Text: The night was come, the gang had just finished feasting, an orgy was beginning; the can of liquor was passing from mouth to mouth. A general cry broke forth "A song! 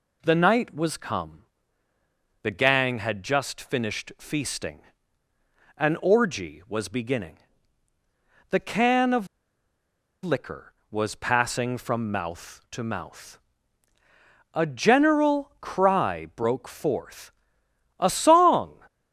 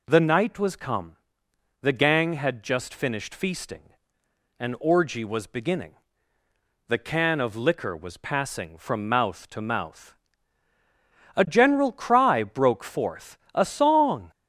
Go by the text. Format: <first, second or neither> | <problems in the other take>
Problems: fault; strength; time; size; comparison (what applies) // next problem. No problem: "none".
second | pauses between "of" and "liquor"; at 9.2 s; 0.98 s long // pauses between "forth" and "A"; noticeable; at 17.3 s; 0.66 s long; slight in the second